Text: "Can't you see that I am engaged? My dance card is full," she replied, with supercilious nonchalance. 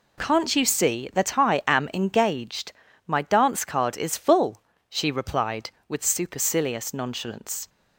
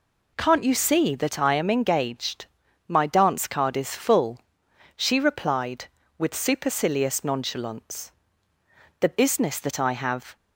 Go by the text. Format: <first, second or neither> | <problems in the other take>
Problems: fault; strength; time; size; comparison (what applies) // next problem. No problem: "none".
first | goes on to say "The business that I have"; from 8.9 s on; 1.3 s long